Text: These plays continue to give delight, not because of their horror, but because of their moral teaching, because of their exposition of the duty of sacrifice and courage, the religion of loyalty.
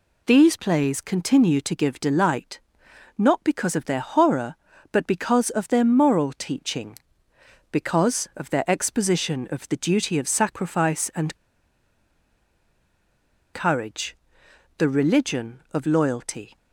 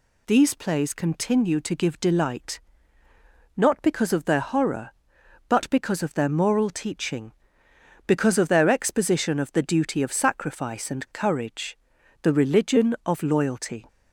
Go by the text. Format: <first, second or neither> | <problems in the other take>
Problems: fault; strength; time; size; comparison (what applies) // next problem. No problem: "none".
second | pauses between "and" and "courage"; strong; at 11.3 s; 2.1 s long